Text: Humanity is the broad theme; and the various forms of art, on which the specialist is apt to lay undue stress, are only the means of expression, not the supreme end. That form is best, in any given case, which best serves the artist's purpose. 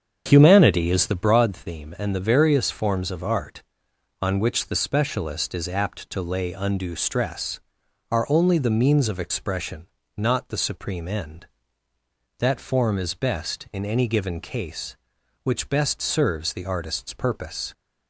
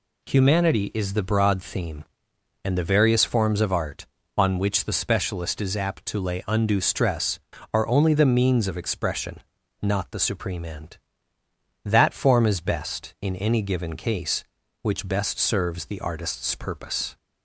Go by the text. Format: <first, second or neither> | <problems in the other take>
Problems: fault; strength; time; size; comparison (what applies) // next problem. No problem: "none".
second | starts louder than the rest; strong; until 1.3 s; 7.5 dB